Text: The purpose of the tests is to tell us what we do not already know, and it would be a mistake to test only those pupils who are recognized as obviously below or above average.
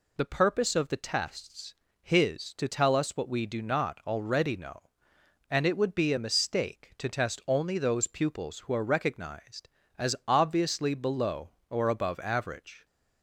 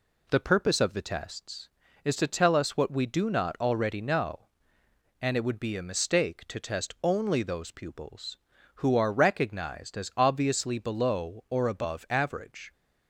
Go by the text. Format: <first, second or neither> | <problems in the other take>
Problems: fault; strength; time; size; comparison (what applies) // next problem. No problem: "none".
second | says "his" for "is"; at 2.0 s